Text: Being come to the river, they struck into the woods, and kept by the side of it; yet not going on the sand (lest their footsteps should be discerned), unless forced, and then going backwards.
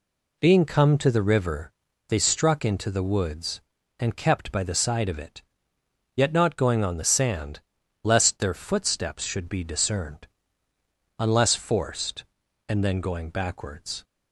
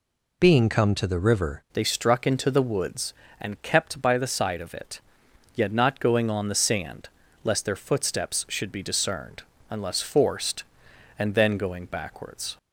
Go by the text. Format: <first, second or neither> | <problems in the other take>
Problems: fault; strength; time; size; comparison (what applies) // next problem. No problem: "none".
first | changes voice at "they"; from 1.7 s on; 10.8 s long